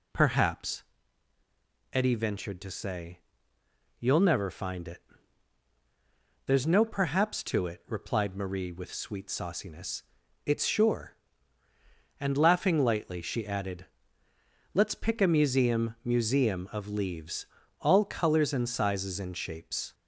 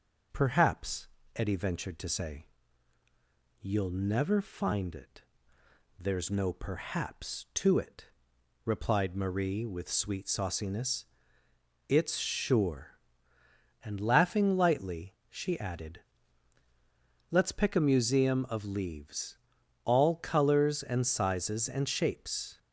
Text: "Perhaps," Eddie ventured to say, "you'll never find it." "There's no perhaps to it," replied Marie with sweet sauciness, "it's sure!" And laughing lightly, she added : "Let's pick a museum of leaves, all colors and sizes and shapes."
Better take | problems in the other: second | says "museum" twice; at 16.0 s

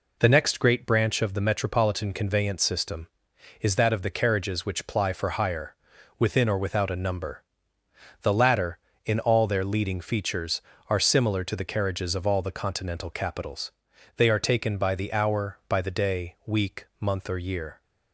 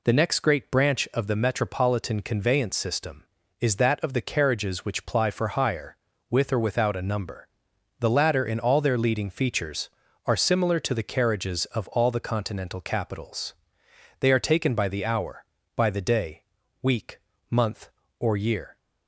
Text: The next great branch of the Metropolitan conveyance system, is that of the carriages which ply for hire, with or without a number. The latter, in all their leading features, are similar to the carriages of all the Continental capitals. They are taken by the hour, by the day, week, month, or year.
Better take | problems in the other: second | says "within" for "with"; at 6.1 s

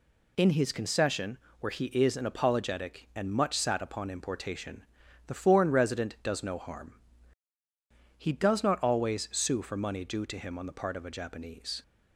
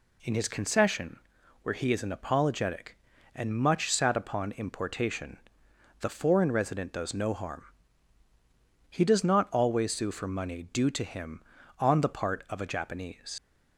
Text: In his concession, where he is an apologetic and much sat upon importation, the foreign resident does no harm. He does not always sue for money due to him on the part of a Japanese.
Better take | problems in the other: first | leaves "Japanese" unfinished; at 13.3 s; 100 ms

